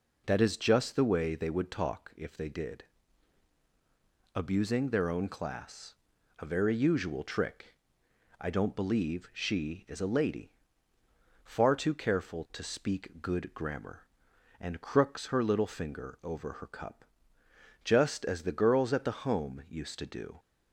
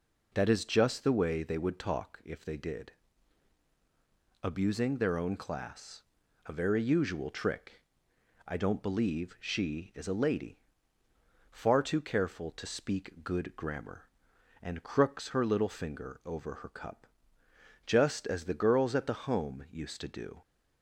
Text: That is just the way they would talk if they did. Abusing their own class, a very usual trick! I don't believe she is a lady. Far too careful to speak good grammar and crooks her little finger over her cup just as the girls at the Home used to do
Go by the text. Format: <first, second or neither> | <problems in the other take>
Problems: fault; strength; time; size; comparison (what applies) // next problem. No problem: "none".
neither | pauses between "cup" and "just"; noticeable; the same in both